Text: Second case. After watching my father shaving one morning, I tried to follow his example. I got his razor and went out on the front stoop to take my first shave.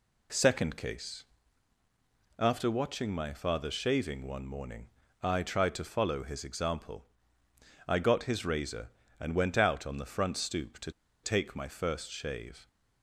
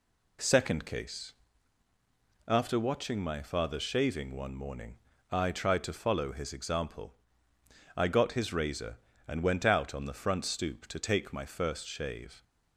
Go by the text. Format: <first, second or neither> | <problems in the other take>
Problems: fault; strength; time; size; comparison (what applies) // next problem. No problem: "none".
second | pauses between "to" and "take"; slight; at 10.9 s; 0.32 s long